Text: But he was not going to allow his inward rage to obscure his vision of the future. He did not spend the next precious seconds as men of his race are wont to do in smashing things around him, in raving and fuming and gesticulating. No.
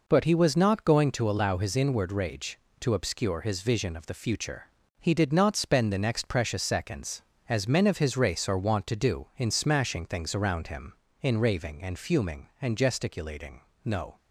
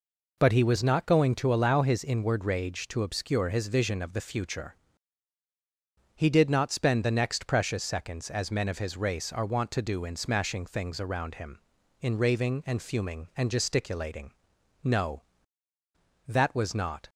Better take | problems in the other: first | goes on to say "That was not"; noticeable; from 16.2 s on; 0.82 s long

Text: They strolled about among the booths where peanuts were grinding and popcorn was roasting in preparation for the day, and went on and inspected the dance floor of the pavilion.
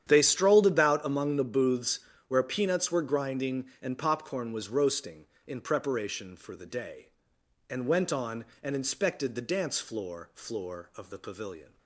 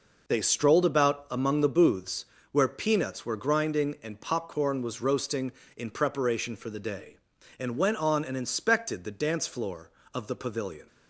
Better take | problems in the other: second | starts louder than the rest; strong; until 1.0 s; 9.5 dB // pauses between "booths" and "where"; slight; at 1.9 s; 0.28 s long; slight in the second // says "floor" twice; at 10.3 s

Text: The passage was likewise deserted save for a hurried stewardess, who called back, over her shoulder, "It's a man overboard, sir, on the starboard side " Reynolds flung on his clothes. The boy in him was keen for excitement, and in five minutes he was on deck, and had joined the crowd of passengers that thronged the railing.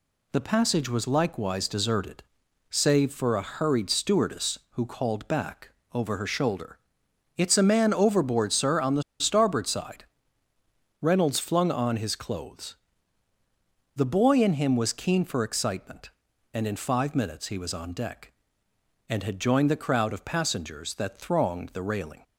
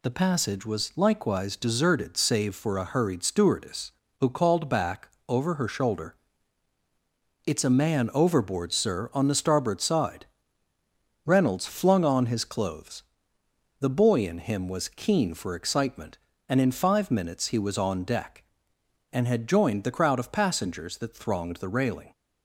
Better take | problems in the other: second | pauses between "deserted" and "save"; noticeable; at 2.2 s; 0.48 s long // pauses between "the" and "starboard"; slight; at 9.0 s; 0.18 s long

